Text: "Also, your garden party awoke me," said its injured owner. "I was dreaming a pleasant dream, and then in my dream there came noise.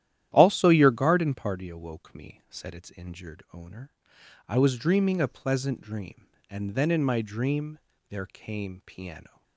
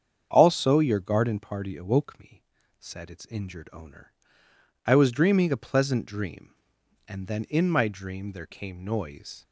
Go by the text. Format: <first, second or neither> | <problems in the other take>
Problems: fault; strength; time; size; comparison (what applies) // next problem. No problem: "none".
second | starts louder than the rest; strong; until 1.3 s; 12 dB; strong in the second // pauses between "dream" and "there"; slight; at 7.7 s; 0.32 s long // says "piano" for "noise"; at 8.8 s